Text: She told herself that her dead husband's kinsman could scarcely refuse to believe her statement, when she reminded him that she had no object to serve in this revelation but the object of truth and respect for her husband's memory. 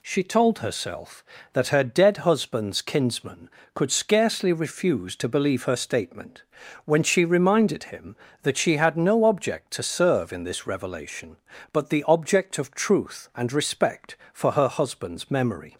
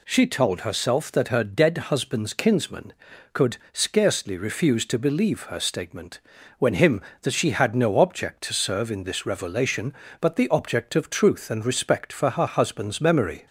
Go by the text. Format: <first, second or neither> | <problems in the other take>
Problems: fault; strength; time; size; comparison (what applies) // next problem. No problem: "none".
first | pauses between "could" and "scarcely"; slight; at 3.5 s; 0.16 s long // skips "she reminded"; at 6.7 s